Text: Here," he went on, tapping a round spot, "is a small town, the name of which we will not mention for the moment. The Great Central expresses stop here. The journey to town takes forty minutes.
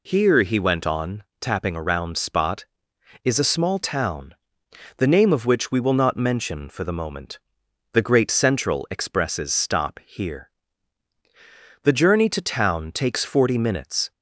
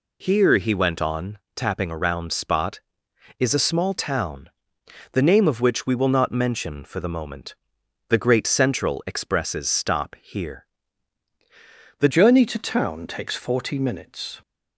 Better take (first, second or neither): first